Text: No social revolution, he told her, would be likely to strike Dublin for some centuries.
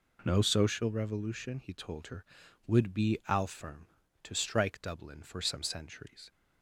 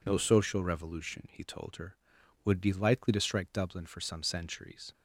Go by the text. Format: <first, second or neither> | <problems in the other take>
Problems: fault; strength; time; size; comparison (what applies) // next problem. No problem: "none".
second | says "alfirm" for "likely"; at 3.2 s